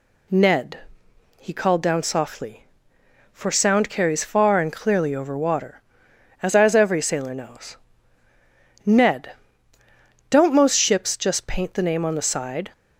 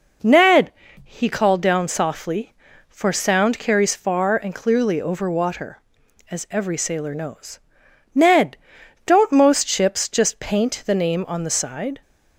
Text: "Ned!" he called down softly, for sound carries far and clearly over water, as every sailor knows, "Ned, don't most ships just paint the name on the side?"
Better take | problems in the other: second | says "as" twice; at 6.5 s

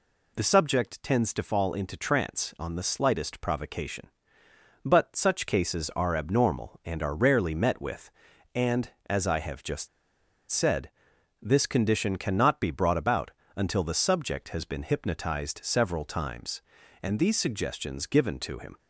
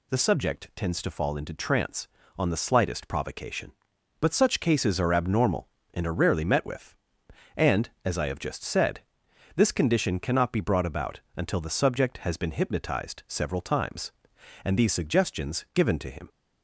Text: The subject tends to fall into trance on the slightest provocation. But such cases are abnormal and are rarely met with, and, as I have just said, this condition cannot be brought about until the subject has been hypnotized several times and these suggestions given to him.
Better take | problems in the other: second | pauses between "just" and "said"; noticeable; at 9.8 s; 0.63 s long // pauses between "about" and "until"; slight; at 13.3 s; 0.24 s long; slight in the second

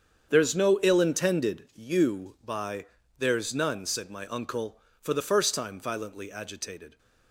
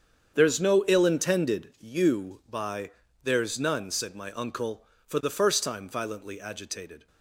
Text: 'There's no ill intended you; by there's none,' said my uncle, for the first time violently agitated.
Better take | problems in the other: neither | starts louder than the rest; strong; the same in both // pauses between "by" and "there's"; slight; the same in both

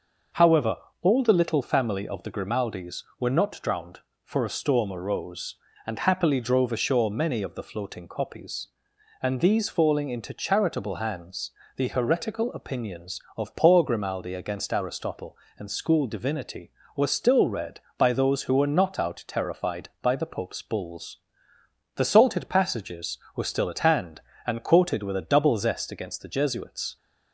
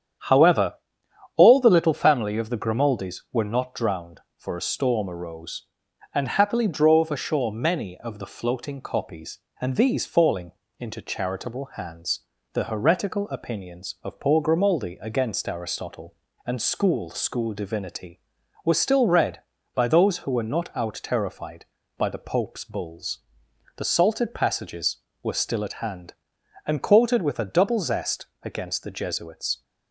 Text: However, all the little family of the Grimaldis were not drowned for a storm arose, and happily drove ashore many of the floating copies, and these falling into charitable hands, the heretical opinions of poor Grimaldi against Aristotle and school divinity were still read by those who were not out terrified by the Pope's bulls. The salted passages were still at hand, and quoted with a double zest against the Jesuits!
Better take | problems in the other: first | starts louder than the rest; strong; until 1.8 s; 9 dB; also in the first // pauses between "falling" and "into"; slight; at 10.5 s; 0.28 s long // says "school" twice; at 17.1 s // pauses between "zest" and "against"; slight; at 28.2 s; 0.16 s long

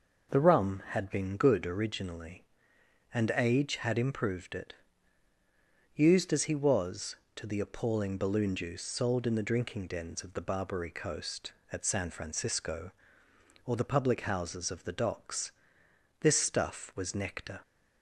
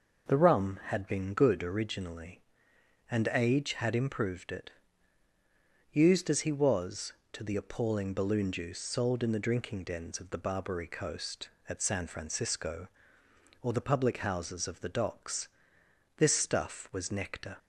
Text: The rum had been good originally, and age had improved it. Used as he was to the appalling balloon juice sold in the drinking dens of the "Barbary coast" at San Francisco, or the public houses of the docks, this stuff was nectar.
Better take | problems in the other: neither | none

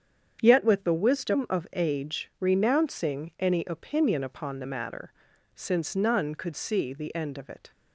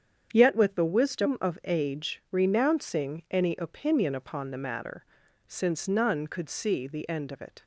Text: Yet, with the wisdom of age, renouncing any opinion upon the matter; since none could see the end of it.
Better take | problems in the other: neither | starts louder than the rest; strong; the same in both

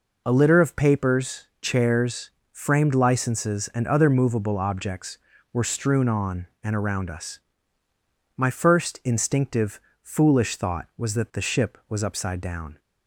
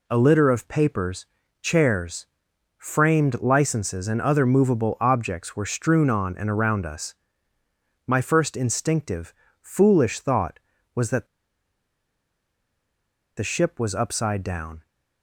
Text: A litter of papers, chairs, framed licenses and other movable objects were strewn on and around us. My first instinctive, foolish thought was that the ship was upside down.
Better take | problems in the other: first | pauses between "that" and "the"; strong; at 11.2 s; 2.1 s long

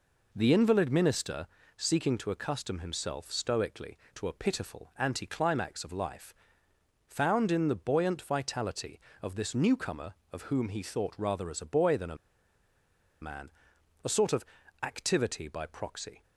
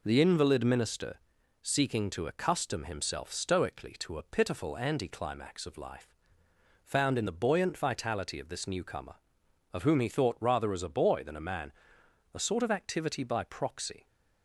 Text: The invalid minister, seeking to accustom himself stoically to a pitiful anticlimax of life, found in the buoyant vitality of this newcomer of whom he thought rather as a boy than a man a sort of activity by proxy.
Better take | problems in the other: second | pauses between "a" and "man"; at 12.1 s; 1.0 s long // pauses between "man" and "a"; noticeable; at 13.4 s; 0.52 s long; noticeable in the second // pauses between "of" and "activity"; slight; at 14.4 s; 0.36 s long

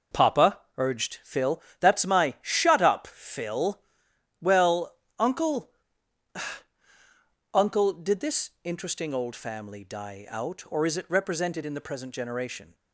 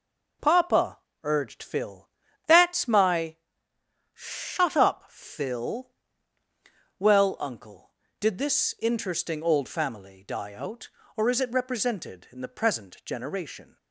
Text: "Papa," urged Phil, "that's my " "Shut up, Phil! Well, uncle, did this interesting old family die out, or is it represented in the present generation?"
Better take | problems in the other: second | says "uncle" twice; at 7.5 s

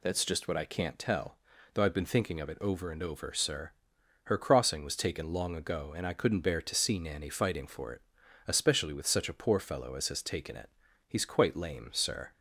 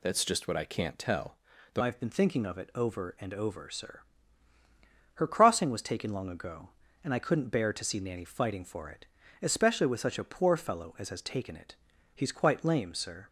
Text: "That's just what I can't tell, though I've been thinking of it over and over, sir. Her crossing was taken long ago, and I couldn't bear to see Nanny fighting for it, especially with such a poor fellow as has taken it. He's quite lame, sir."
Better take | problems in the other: first | changes voice at "I've"; from 1.7 s on; 11.5 s long

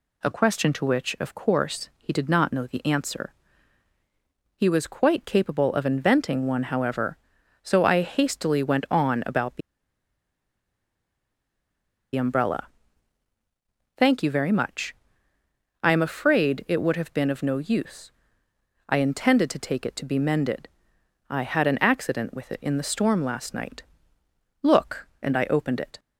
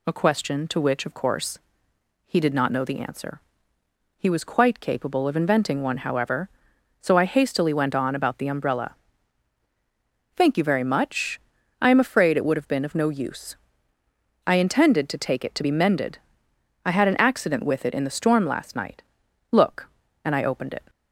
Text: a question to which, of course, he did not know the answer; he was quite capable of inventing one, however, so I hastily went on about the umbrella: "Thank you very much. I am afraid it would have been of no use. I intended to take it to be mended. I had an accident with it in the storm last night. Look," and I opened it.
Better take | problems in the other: second | pauses between "the" and "umbrella"; strong; at 9.6 s; 2.5 s long

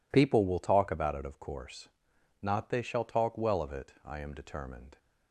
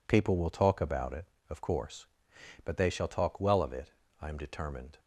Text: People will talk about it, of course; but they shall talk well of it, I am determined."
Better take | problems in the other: second | says "not" for "but"; at 2.4 s

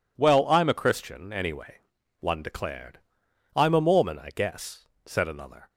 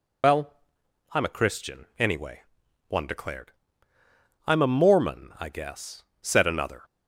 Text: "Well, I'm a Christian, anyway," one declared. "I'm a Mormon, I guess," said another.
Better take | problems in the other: first | loses the start of "Well"; at 0.2 s; 75 ms

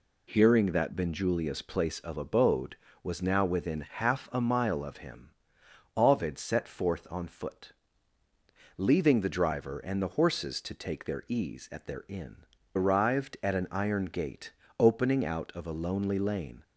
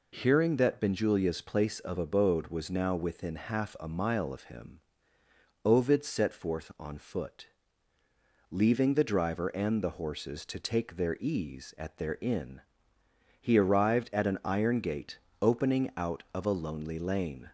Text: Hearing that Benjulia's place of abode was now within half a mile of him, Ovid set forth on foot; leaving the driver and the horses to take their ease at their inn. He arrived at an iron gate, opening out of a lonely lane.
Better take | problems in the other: second | skips "He"; at 12.5 s

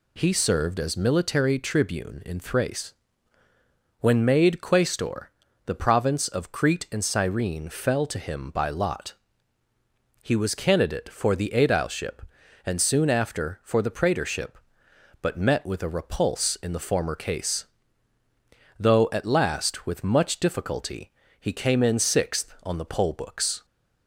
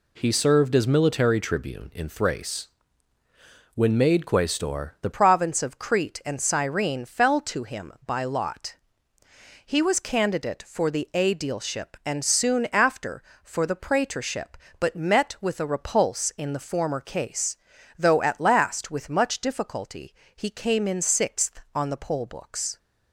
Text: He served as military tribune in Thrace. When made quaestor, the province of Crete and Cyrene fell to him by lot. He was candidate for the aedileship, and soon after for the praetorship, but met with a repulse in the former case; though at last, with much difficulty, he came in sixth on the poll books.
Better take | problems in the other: first | changes voice at "province"; from 5.1 s on; 17.6 s long

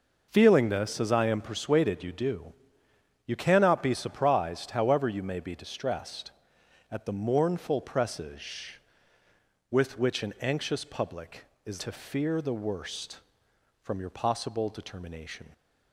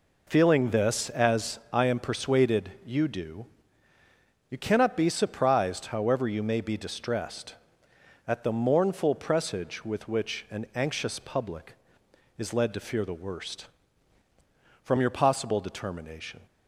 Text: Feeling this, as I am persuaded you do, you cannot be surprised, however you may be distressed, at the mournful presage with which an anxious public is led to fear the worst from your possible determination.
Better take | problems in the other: second | skips "led"; at 11.8 s

